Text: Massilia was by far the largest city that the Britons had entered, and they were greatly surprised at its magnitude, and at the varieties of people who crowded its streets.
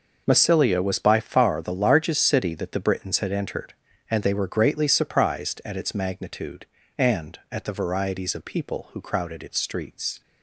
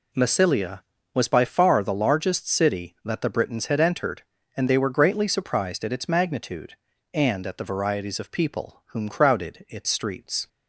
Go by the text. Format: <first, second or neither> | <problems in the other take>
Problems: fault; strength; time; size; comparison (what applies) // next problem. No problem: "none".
first | says "whom" for "who"; at 8.8 s